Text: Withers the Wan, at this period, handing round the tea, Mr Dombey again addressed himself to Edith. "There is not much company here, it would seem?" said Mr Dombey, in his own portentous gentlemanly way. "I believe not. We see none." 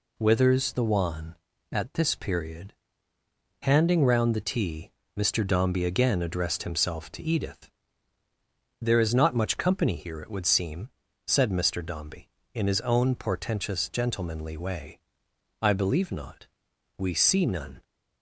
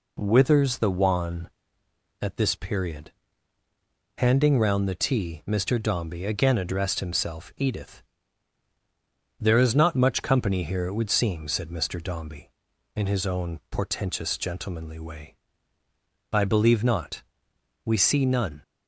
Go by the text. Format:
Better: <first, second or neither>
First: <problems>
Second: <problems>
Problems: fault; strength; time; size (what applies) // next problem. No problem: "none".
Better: first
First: none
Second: skips "to"; at 7.5 s